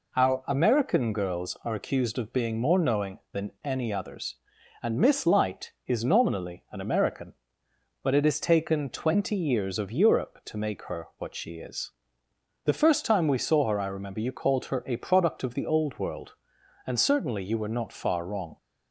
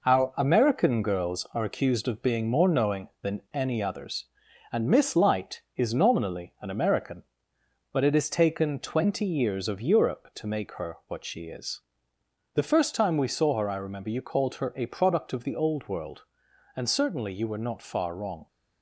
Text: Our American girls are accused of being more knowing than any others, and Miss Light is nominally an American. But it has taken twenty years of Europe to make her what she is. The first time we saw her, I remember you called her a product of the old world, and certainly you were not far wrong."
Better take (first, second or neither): first